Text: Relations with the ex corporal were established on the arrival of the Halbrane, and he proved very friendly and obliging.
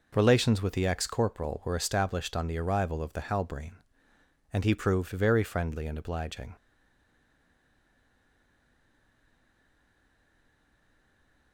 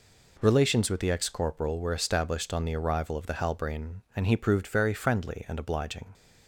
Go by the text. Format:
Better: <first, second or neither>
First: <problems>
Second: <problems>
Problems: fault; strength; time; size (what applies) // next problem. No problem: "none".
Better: second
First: stays silent after the last word; strong; from 6.5 s on; 5.0 s long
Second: none